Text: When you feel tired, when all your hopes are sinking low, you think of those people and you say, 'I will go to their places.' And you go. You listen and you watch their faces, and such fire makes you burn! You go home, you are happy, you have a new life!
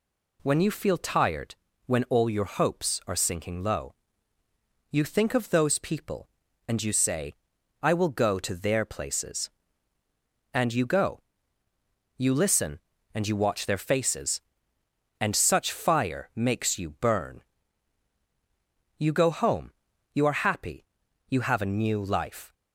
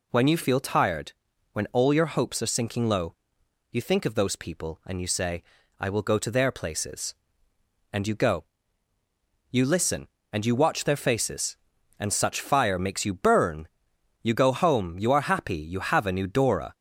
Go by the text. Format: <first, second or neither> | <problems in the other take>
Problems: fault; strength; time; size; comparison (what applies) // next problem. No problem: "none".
first | says "dora" for "life"; at 16.2 s